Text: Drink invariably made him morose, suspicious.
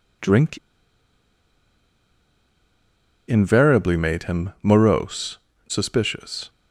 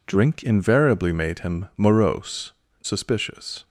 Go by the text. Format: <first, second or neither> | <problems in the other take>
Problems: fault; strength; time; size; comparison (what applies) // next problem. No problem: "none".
second | pauses between "Drink" and "invariably"; strong; at 0.5 s; 2.6 s long